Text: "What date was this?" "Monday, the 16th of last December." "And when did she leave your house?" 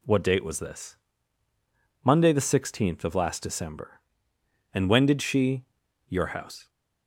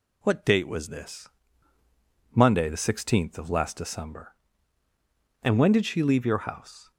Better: second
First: skips "leave"; at 5.8 s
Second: none

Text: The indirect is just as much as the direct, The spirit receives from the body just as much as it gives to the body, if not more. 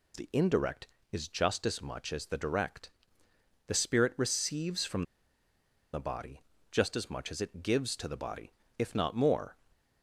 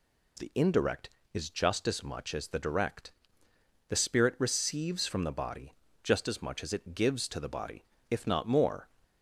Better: second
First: pauses between "from" and "the"; noticeable; at 5.0 s; 0.89 s long // pauses between "body" and "just"; slight; at 6.3 s; 0.32 s long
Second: pauses between "body" and "just"; slight; at 5.7 s; 0.32 s long

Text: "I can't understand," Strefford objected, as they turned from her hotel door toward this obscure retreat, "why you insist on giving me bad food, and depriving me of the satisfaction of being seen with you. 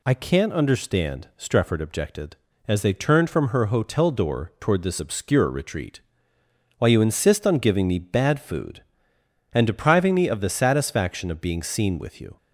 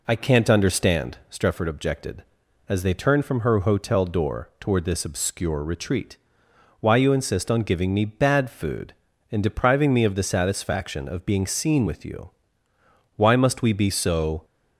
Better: first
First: none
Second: goes on to say "Why must we be so"; noticeable; from 13.1 s on; 1.2 s long

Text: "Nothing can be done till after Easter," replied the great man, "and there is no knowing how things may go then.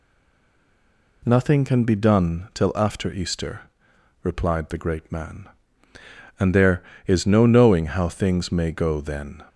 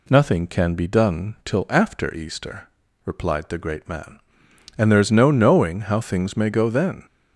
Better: second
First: stays silent before the first word; noticeable; until 1.2 s; 1.2 s long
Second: none

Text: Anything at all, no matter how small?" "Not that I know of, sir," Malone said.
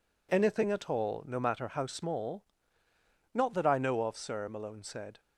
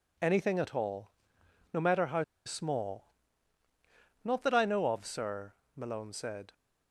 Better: first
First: none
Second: pauses between "how" and "small"; slight; at 2.2 s; 0.22 s long

